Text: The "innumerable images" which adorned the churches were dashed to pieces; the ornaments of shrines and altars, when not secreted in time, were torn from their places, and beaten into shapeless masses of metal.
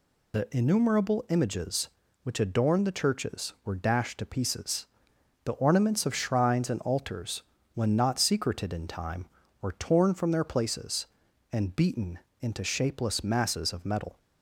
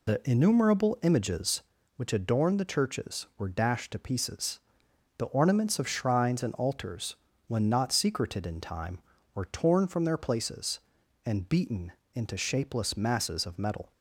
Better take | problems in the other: first | starts louder than the rest; slight; until 1.6 s; 2 dB // pauses between "beaten" and "into"; slight; at 11.9 s; 0.22 s long; slight in the first

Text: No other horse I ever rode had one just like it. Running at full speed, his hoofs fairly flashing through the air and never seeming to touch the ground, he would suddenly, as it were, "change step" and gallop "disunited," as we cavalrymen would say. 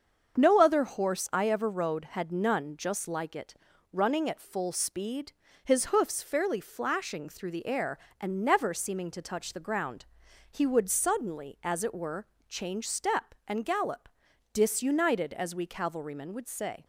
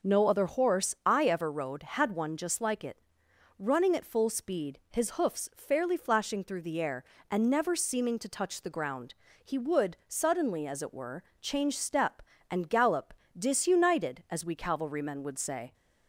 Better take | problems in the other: second | starts louder than the rest; until 1.4 s; 7 dB; noticeable in the second // says "none" for "one"; at 2.3 s // pauses between "gallop" and "disunited"; at 14.1 s; 0.42 s long; slight in the second

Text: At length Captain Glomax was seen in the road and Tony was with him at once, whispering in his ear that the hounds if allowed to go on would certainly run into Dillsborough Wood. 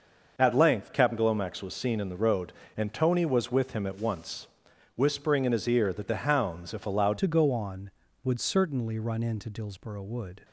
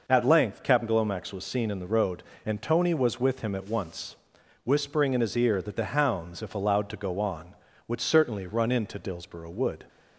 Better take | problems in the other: second | starts louder than the rest; noticeable; until 1.3 s; 6 dB // changes voice at "to"; from 7.1 s on; 3.3 s long

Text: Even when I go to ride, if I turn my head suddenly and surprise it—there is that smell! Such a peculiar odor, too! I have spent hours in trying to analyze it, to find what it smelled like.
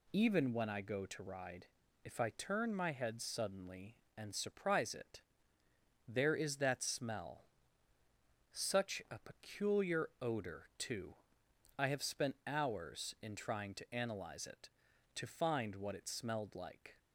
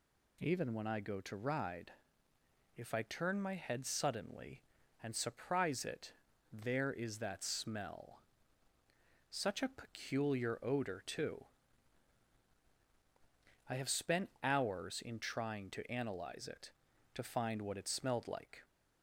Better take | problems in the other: neither | none

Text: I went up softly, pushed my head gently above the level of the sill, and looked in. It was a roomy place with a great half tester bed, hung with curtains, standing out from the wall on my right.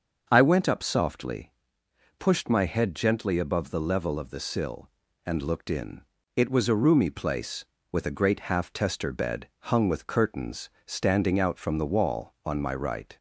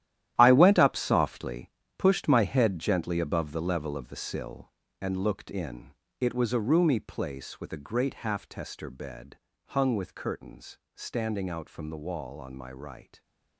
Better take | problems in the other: first | gets quieter; strong; throughout; 12.5 dB // starts louder than the rest; strong; until 1.3 s; 12.5 dB; also in the first

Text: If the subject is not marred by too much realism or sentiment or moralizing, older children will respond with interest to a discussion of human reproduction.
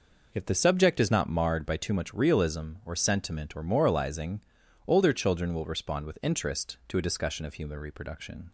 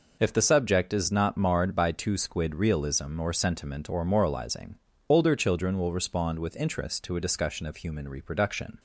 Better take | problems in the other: first | says "squid" for "much"; at 2.1 s

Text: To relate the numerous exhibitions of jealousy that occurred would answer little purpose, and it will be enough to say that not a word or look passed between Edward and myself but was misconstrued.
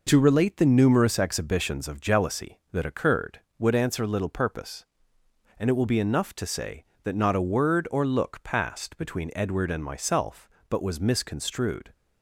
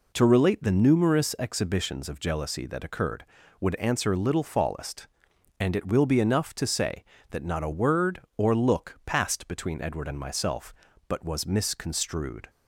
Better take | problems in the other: first | says "fallest" for "purpose"; at 4.4 s

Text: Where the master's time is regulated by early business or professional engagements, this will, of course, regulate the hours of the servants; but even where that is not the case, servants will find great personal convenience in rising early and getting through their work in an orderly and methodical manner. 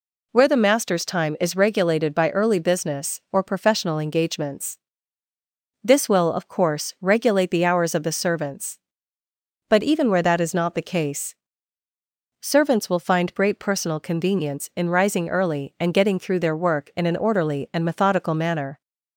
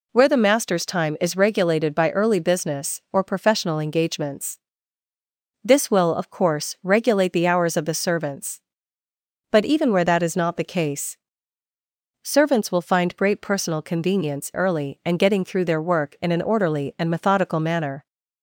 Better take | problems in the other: first | skips "in rising"; at 14.5 s

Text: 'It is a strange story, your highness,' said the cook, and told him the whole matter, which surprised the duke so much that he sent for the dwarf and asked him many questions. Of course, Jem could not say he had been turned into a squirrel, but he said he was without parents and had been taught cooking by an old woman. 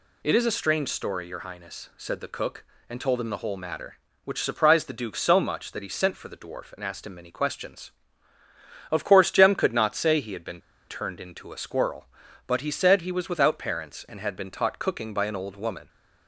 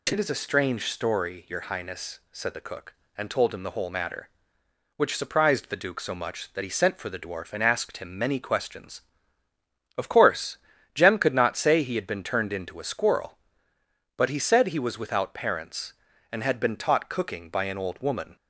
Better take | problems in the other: second | pauses between "been" and "turned"; slight; at 10.6 s; 0.28 s long

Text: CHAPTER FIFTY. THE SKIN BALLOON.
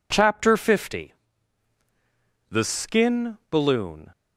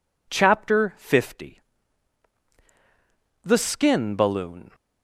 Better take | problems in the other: neither | none

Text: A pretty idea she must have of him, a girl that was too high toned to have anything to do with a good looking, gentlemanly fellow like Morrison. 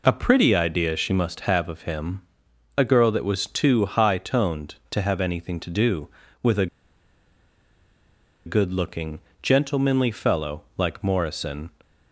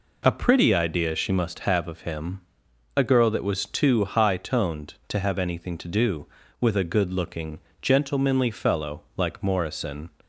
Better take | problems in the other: second | pauses between "a" and "good"; strong; at 6.6 s; 1.7 s long // pauses between "fellow" and "like"; slight; at 10.6 s; 0.16 s long; slight in the second

